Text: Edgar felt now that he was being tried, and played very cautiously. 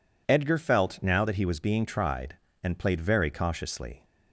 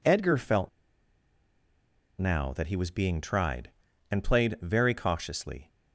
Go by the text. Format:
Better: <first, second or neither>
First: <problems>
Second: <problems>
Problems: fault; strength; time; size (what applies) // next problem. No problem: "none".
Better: first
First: none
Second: pauses between "felt" and "now"; strong; at 0.6 s; 1.4 s long